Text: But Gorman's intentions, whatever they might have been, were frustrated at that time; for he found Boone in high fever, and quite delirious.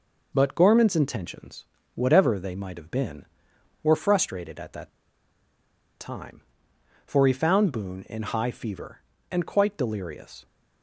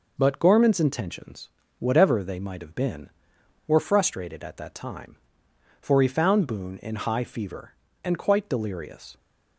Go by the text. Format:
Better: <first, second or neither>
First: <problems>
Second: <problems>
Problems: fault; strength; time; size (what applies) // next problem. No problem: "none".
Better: second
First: pauses between "that" and "time"; at 4.8 s; 1.1 s long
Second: none